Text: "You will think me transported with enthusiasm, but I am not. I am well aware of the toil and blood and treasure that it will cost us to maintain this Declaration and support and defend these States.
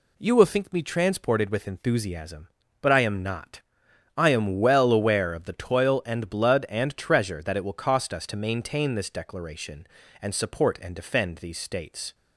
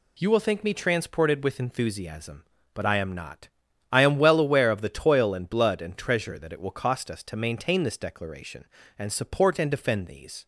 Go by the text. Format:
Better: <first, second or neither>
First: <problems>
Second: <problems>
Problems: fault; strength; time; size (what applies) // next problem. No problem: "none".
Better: first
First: none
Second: stops before "States"; at 10.4 s